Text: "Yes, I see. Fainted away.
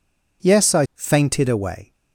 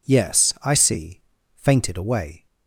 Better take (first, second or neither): second